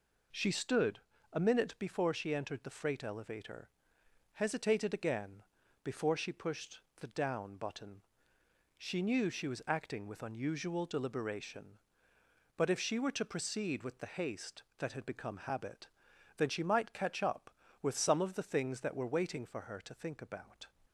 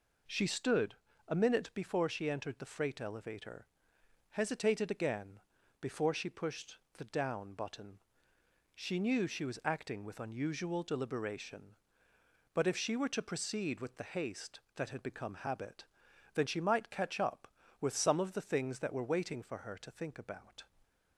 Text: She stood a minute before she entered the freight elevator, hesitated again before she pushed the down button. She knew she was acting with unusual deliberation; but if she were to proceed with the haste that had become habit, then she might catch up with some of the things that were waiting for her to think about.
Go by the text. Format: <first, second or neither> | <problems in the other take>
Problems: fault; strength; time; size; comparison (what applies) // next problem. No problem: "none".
neither | pauses between "stood" and "a"; slight; the same in both // pauses between "again" and "before"; the same in both // pauses between "pushed" and "the"; slight; the same in both